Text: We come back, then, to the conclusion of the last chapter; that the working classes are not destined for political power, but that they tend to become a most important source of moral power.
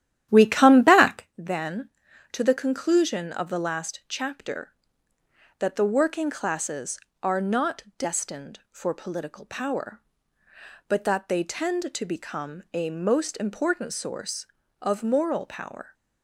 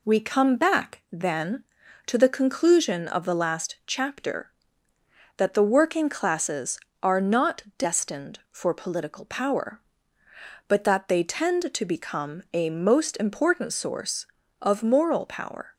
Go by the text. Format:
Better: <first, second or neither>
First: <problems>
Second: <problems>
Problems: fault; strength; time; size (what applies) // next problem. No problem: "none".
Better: second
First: starts louder than the rest; strong; until 1.3 s; 11.5 dB // pauses between "not" and "destined"; slight; at 7.8 s; 0.16 s long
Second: pauses between "not" and "destined"; slight; at 7.6 s; 0.16 s long